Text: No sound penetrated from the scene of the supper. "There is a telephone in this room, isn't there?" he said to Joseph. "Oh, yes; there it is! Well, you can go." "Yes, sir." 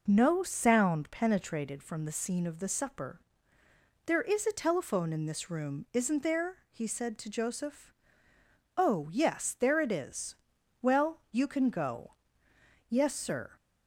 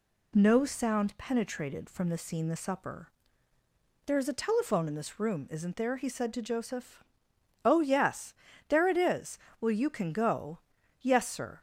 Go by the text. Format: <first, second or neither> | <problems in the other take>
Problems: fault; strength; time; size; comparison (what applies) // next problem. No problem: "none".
first | skips "of"; at 2.4 s